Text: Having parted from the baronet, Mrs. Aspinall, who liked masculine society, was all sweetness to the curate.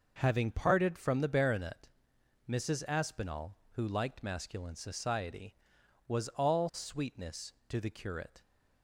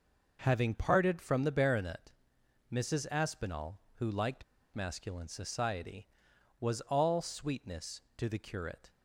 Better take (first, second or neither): first